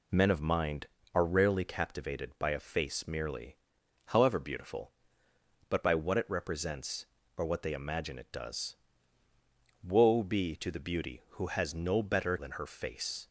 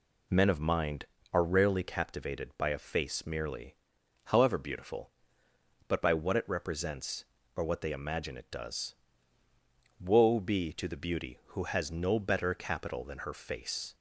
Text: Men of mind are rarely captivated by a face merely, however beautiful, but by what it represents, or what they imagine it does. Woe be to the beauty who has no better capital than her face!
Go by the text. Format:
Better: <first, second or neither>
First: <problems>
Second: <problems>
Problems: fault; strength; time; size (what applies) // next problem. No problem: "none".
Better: second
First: skips "capital"; at 12.3 s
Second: none